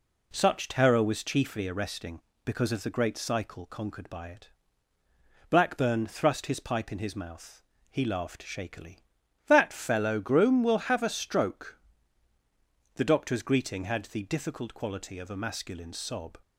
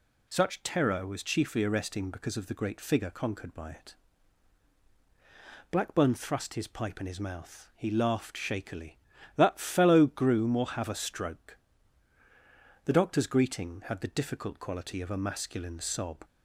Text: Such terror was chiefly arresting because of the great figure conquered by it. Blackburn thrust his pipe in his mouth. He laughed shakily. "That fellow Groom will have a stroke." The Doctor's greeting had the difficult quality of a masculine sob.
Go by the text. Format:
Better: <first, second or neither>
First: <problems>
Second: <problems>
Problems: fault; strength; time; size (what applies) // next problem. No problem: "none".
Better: second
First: says "cycle" for "figure"; at 3.1 s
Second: none